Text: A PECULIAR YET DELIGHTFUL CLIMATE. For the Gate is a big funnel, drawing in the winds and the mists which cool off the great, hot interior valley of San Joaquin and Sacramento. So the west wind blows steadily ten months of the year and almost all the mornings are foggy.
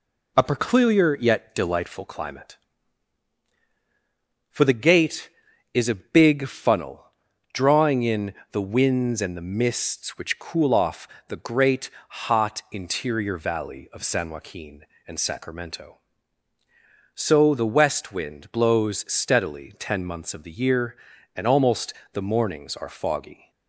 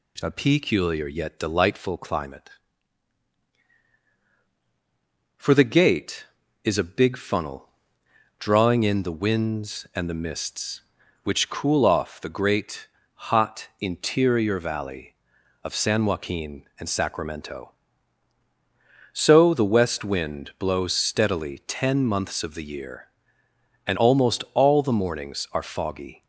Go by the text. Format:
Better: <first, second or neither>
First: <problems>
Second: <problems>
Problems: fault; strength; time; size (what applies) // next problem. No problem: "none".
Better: second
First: pauses between "in" and "the"; slight; at 8.3 s; 0.16 s long // pauses between "off" and "the"; slight; at 11.0 s; 0.22 s long // skips "all"; at 22.0 s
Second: none